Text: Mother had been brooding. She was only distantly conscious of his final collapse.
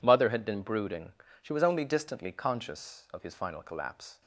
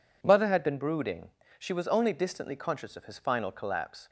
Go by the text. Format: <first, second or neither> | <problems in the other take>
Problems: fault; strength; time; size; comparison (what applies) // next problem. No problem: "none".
neither | none